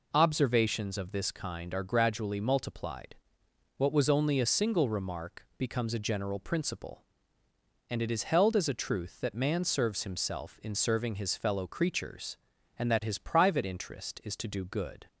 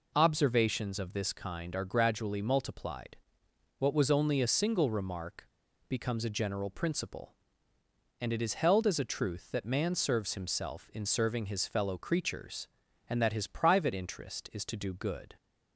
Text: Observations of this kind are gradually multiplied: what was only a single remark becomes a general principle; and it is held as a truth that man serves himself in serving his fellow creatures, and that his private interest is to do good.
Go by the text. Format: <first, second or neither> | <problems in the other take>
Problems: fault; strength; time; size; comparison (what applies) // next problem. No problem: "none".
first | pauses between "remark" and "becomes"; at 5.4 s; 0.41 s long